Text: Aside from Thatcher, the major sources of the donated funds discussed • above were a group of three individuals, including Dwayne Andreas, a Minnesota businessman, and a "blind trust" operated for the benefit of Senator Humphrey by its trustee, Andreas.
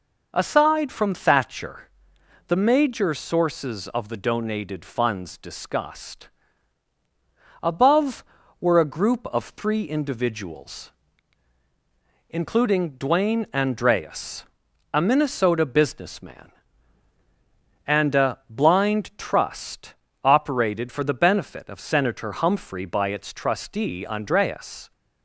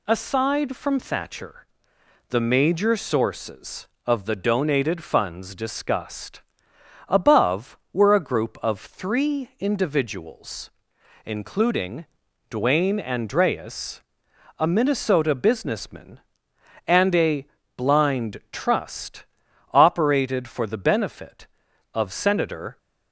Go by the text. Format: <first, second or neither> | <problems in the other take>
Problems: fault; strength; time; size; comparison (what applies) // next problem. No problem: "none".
first | pauses between "including" and "Dwayne"; at 12.0 s; 0.44 s long // pauses between "a" and "blind"; slight; at 17.4 s; 0.30 s long // pauses between "trust" and "operated"; noticeable; at 19.2 s; 0.46 s long; slight in the first // stops before "Humphrey by its trustee Andreas"; at 22.7 s